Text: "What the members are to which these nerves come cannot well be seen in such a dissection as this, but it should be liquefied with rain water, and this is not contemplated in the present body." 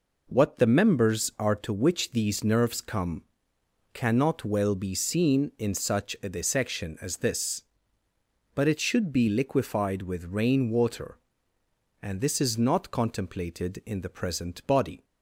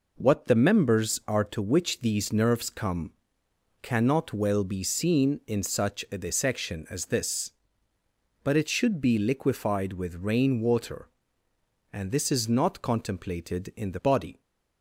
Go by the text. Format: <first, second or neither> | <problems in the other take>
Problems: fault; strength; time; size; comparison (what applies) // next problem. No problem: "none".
first | pauses between "come" and "cannot"; noticeable; at 3.1 s; 0.70 s long; noticeable in the first // skips "present"; at 14.0 s